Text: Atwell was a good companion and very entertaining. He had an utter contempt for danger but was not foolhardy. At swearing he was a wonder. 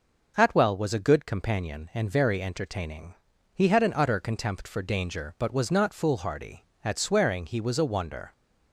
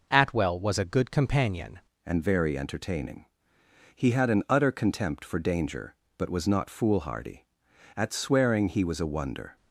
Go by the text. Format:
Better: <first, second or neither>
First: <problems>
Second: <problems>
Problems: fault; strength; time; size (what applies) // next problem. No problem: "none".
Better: first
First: none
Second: changes voice at "and"; from 2.0 s on; 7.5 s long